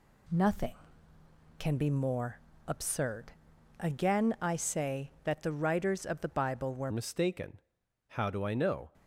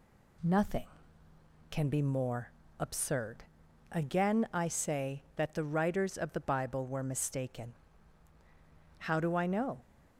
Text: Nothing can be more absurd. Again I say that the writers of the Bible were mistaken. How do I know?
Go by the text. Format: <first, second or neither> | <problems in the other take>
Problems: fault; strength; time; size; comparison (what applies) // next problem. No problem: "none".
second | pauses between "more" and "absurd"; slight; at 2.3 s; 0.28 s long; slight in the second // changes voice at "mistaken"; from 6.9 s on; 2.0 s long